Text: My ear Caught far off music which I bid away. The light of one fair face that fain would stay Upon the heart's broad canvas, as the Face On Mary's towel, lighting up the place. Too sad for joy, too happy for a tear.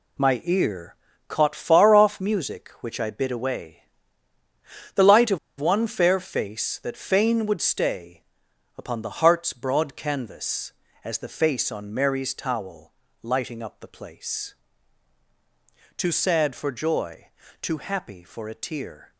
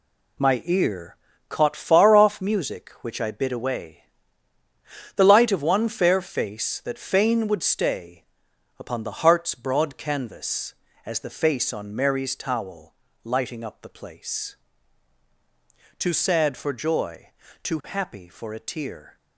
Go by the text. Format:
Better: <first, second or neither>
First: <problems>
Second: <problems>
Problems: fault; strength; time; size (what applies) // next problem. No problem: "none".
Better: second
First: pauses between "ear" and "Caught"; slight; at 0.9 s; 0.34 s long // pauses between "of" and "one"; slight; at 5.3 s; 0.21 s long // pauses between "stay" and "Upon"; noticeable; at 8.2 s; 0.52 s long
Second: pauses between "ear" and "Caught"; slight; at 1.1 s; 0.34 s long // pauses between "stay" and "Upon"; noticeable; at 8.2 s; 0.52 s long